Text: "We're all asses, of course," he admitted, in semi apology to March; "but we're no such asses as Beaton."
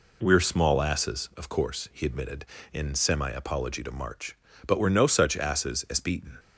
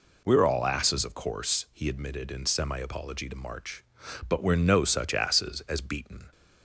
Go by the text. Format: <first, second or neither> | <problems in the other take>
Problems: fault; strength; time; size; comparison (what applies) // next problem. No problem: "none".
second | says "small" for "all"; at 0.3 s